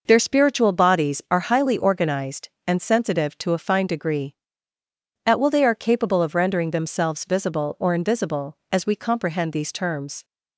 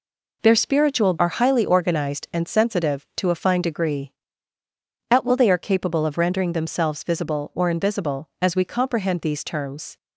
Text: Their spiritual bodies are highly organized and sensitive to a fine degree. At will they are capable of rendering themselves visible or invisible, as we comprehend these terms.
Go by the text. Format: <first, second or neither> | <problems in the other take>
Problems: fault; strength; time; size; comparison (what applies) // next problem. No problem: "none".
first | skips "bodies"; at 1.1 s